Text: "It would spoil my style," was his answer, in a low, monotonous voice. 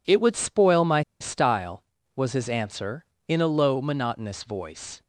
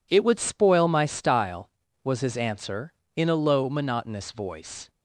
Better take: second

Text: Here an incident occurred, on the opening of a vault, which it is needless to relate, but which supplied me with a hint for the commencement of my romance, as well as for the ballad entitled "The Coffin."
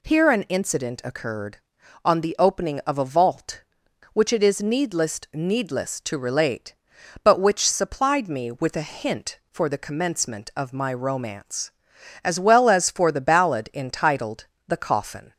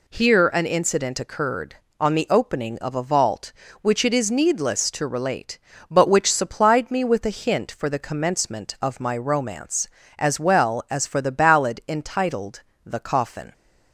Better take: second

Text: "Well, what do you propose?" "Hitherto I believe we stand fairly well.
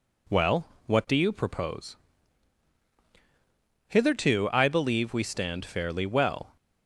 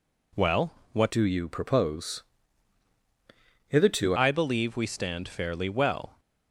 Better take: first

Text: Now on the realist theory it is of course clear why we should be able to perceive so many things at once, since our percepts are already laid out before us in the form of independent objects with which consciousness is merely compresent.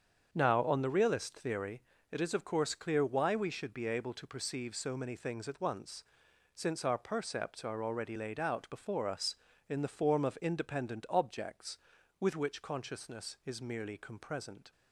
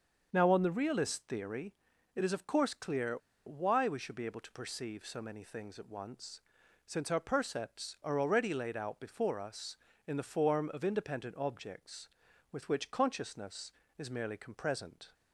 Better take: first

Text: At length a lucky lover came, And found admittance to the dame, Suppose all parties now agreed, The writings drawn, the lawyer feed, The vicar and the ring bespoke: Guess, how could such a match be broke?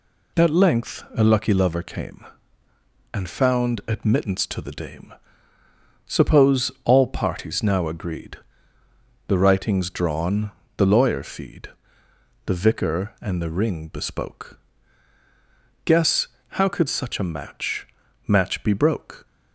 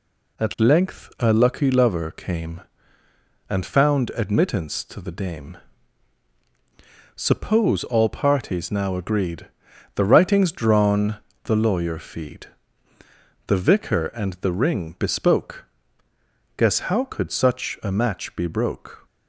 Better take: second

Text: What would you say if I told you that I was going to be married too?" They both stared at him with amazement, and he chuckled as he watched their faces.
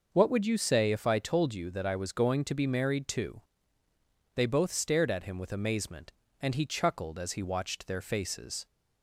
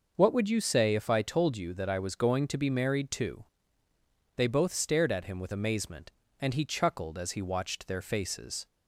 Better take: neither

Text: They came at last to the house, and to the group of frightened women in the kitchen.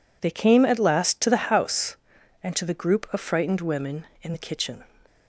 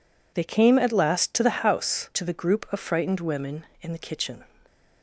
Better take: first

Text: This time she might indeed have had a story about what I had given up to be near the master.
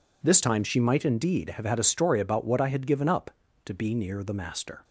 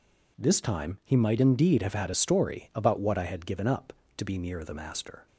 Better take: first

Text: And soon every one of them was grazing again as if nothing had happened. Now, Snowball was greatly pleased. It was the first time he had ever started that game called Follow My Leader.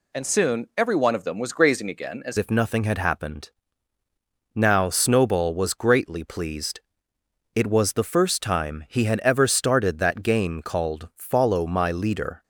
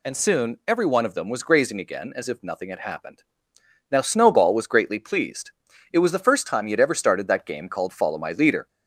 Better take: second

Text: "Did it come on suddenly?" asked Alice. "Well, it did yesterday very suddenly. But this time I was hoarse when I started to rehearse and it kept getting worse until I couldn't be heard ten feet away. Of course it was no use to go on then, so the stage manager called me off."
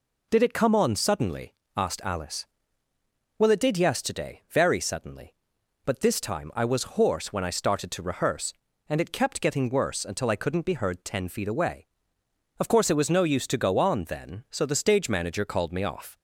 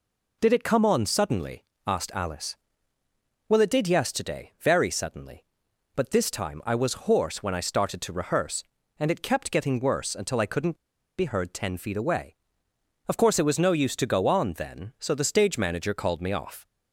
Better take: first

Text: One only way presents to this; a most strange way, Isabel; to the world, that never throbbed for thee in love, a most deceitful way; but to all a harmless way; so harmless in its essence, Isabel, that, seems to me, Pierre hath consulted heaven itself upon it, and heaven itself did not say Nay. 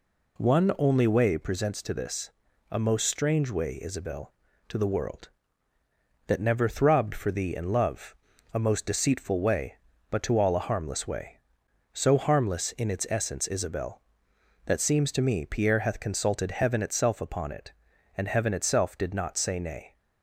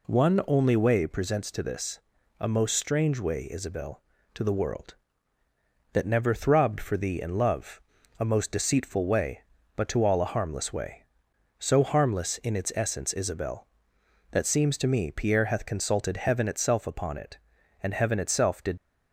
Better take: first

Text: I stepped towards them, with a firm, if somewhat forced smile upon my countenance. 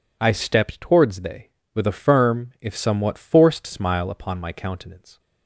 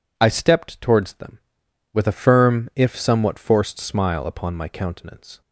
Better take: second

